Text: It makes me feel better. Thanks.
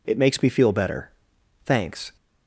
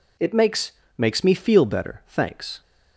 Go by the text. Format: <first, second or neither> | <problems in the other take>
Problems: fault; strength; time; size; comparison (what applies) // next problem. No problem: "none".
first | says "makes" twice; at 0.9 s